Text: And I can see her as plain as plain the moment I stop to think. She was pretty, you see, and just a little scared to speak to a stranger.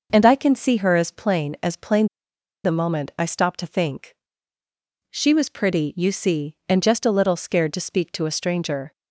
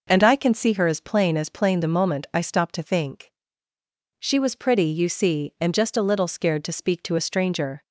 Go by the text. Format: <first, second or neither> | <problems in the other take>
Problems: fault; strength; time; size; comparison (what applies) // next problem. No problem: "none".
second | pauses between "plain" and "the"; noticeable; at 2.0 s; 0.57 s long